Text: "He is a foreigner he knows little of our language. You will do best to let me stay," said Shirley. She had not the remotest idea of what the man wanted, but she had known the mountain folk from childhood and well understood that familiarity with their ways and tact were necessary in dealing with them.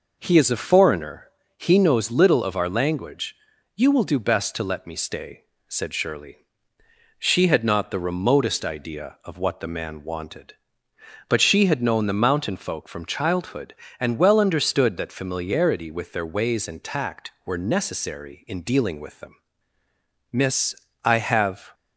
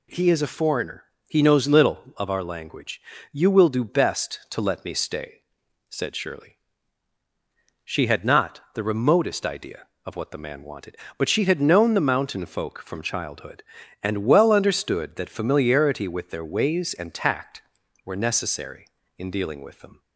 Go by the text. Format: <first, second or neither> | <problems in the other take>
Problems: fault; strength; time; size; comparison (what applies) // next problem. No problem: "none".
second | pauses between "foreigner" and "he"; slight; at 1.2 s; 0.32 s long; slight in the second // goes on to say "Miss I have"; from 20.3 s on; 1.4 s long